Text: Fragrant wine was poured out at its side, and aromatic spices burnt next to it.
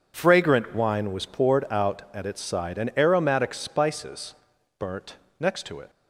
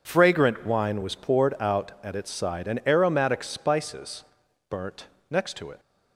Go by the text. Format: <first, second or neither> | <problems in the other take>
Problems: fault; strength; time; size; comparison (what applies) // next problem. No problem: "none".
neither | pauses between "spices" and "burnt"; the same in both // pauses between "burnt" and "next"; slight; the same in both